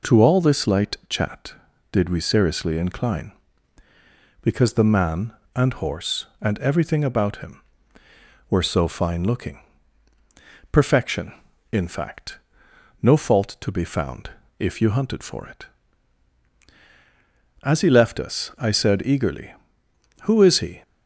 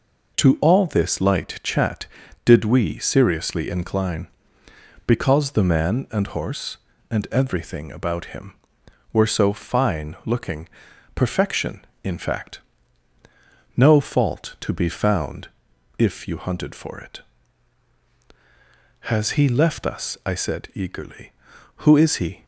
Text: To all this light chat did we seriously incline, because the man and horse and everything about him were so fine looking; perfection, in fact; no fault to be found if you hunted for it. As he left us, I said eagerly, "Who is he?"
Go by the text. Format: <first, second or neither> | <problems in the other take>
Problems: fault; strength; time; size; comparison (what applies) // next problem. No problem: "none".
first | pauses between "found" and "if"; noticeable; at 15.4 s; 0.52 s long; slight in the first // says "Has" for "As"; at 19.1 s